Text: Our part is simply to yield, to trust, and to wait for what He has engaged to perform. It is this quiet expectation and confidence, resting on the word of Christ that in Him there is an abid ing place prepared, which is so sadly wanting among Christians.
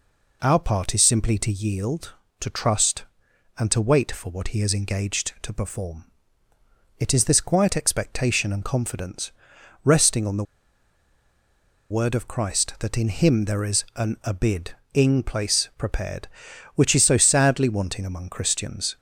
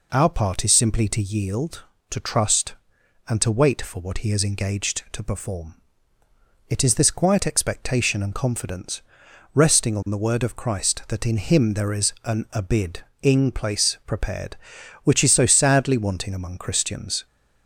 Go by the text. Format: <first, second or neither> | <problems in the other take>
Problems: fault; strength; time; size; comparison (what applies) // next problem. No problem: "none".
second | pauses between "the" and "word"; strong; at 10.4 s; 1.4 s long // pauses between "abid" and "ing"; slight; at 14.6 s; 0.24 s long; slight in the second